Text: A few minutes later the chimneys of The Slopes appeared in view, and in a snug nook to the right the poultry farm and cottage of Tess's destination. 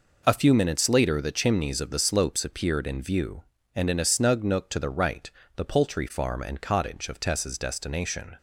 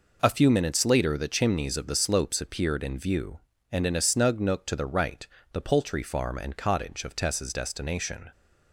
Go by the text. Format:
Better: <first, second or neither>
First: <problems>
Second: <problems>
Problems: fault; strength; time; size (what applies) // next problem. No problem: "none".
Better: neither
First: pauses between "right" and "the"; slight; at 5.3 s; 0.26 s long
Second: pauses between "right" and "the"; slight; at 5.2 s; 0.26 s long